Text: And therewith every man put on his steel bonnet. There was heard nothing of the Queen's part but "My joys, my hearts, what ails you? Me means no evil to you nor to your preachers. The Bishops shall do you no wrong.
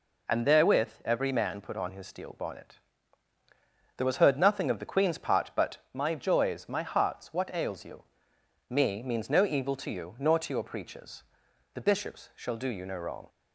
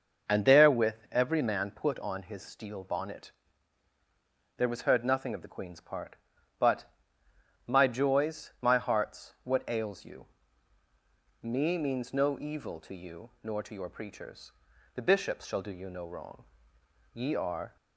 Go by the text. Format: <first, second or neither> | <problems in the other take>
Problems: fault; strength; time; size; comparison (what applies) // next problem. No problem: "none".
first | starts louder than the rest; noticeable; until 1.4 s; 6 dB // pauses between "therewith" and "every"; slight; at 0.9 s; 0.16 s long; slight in the first // pauses between "but" and "My"; noticeable; at 6.8 s; 0.80 s long // goes on to say "Ye are"; noticeable; from 17.1 s on; 0.62 s long